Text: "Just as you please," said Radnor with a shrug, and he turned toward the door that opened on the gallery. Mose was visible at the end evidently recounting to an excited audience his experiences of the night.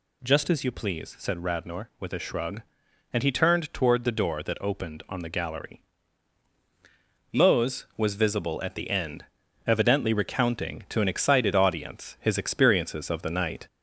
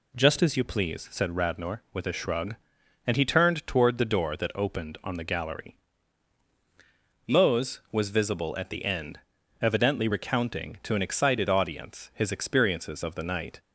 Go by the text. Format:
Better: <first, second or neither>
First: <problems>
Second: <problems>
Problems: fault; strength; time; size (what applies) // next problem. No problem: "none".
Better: second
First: gets louder; slight; throughout; 2.5 dB // pauses between "end" and "evidently"; at 9.2 s; 0.42 s long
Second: pauses between "end" and "evidently"; at 9.1 s; 0.42 s long